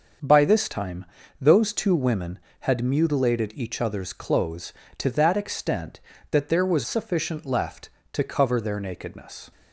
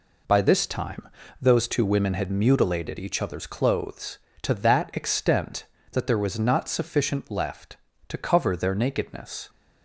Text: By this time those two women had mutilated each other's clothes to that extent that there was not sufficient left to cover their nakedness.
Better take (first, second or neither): second